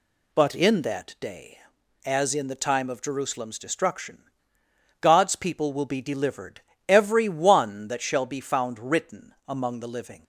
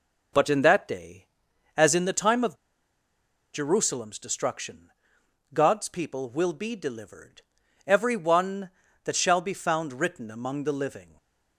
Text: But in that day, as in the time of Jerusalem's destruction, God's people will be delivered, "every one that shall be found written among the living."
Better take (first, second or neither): first